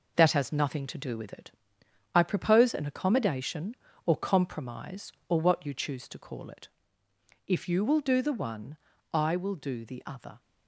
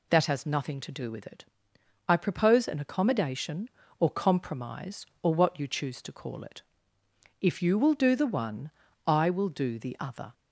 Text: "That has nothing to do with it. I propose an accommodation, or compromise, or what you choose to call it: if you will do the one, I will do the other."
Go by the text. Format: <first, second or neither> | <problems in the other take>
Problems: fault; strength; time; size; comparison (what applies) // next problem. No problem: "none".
second | gets quieter; noticeable; throughout; 5.5 dB